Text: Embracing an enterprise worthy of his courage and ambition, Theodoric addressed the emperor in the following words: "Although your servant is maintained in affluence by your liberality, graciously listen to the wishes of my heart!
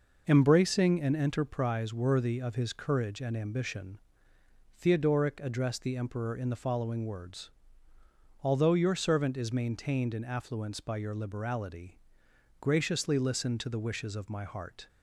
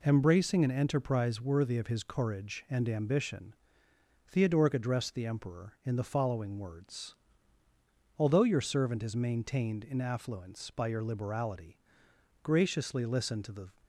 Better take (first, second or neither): first